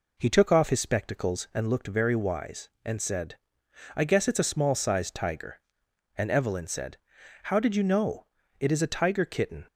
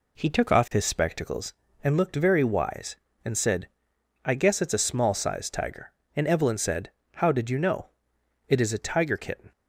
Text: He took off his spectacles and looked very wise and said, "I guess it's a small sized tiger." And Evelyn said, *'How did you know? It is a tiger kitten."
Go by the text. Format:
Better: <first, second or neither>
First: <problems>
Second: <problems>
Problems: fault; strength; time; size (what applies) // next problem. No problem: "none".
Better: neither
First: none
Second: none